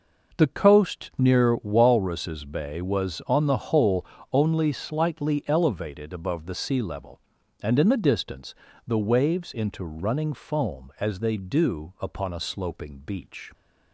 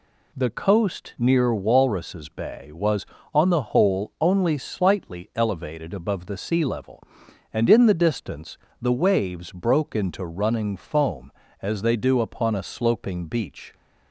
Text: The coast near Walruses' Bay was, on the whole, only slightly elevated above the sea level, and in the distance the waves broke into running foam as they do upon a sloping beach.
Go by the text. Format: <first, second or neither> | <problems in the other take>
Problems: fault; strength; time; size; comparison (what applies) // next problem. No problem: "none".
second | pauses between "distance" and "the"; slight; at 8.5 s; 0.32 s long; slight in the second // skips "broke"; at 9.5 s